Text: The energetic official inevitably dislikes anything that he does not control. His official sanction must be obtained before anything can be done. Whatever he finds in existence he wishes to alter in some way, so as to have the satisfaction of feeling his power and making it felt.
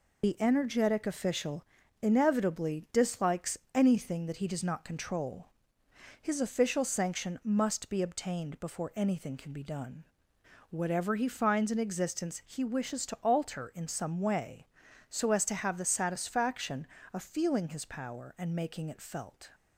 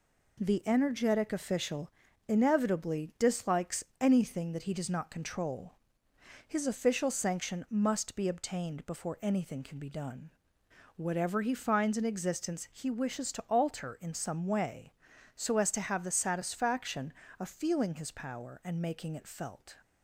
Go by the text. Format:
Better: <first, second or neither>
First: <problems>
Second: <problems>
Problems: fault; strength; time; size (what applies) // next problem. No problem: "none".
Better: second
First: loses the start of "The"; at 0.2 s; 120 ms // pauses between "official" and "inevitably"; at 1.6 s; 0.38 s long // pauses between "dislikes" and "anything"; slight; at 3.5 s; 0.18 s long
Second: pauses between "official" and "inevitably"; at 1.9 s; 0.38 s long // pauses between "dislikes" and "anything"; slight; at 3.8 s; 0.18 s long